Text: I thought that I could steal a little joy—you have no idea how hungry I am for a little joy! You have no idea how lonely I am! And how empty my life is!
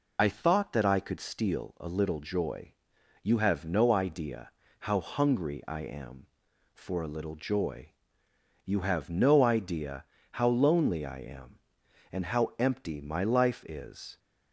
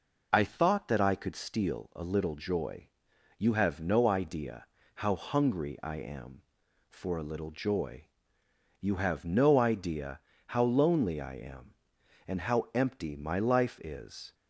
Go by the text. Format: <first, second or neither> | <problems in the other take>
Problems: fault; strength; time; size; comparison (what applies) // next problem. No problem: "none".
second | loses the start of "I"; at 0.1 s; 30 ms // pauses between "idea" and "how"; slight; at 4.5 s; 0.30 s long; slight in the second // pauses between "idea" and "how"; slight; at 10.0 s; 0.28 s long; slight in the second